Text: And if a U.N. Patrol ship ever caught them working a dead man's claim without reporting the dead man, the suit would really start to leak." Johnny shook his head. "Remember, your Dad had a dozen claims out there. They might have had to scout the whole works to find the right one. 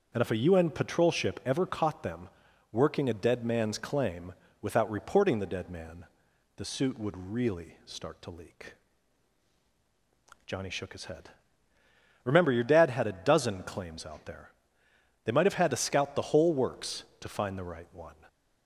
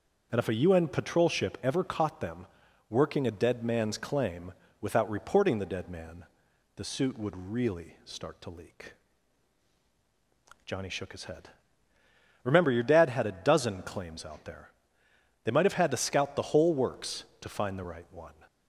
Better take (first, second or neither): neither